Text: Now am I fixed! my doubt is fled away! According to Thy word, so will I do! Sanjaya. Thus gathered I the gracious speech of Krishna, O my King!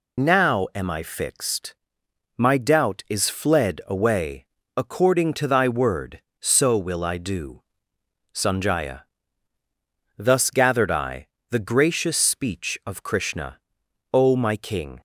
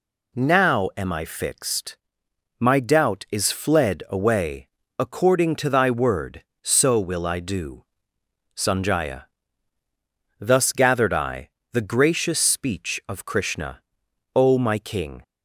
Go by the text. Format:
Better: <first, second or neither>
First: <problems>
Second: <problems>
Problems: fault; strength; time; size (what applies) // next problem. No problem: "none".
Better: second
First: loses the start of "Now"; at 0.1 s; 55 ms // pauses between "I" and "the"; slight; at 11.2 s; 0.22 s long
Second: pauses between "I" and "the"; slight; at 11.5 s; 0.22 s long